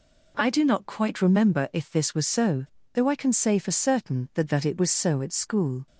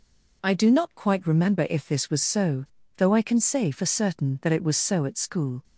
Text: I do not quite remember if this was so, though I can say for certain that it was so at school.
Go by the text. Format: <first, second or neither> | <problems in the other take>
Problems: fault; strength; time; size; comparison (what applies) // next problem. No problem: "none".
second | says "that" twice; at 4.5 s